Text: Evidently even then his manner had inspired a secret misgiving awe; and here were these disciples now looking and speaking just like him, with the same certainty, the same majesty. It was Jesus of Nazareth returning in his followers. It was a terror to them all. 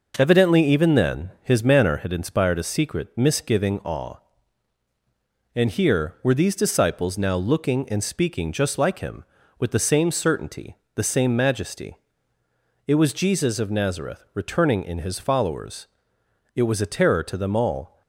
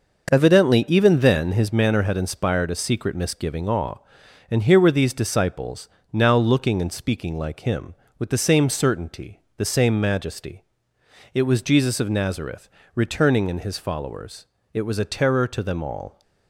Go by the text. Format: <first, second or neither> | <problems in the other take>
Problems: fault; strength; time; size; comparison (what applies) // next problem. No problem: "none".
first | starts louder than the rest; noticeable; until 1.3 s; 6 dB // pauses between "disciples" and "now"; slight; at 5.8 s; 0.24 s long // skips "just"; at 7.3 s // pauses between "Nazareth" and "returning"; slight; at 12.6 s; 0.24 s long